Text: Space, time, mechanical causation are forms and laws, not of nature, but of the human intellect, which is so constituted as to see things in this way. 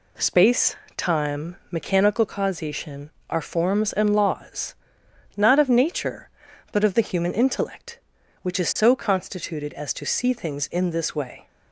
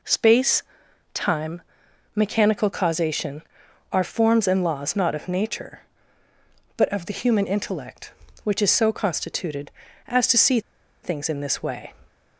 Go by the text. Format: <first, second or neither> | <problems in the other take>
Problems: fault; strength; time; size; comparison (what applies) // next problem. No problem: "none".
first | pauses between "see" and "things"; at 10.5 s; 0.43 s long